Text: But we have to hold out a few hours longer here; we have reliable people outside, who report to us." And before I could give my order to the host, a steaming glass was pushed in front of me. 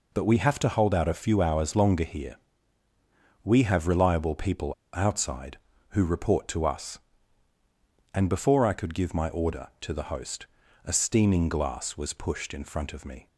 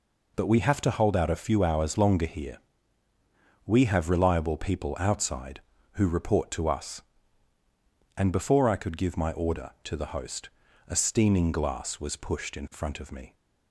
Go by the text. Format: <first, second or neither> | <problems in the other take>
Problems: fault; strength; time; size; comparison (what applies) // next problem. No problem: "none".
second | pauses between "people" and "outside"; slight; at 4.7 s; 0.21 s long